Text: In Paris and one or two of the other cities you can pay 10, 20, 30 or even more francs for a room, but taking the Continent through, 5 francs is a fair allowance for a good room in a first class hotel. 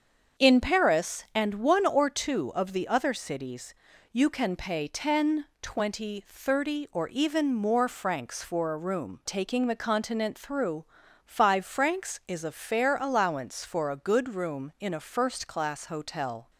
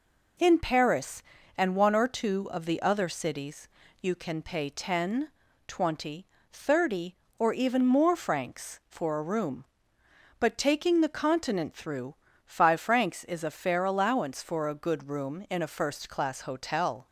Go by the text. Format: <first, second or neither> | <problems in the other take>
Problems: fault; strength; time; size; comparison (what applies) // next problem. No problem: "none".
second | starts louder than the rest; until 1.4 s; 7 dB // pauses between "cities" and "you"; at 3.7 s; 0.40 s long; slight in the second // skips "but"; at 9.2 s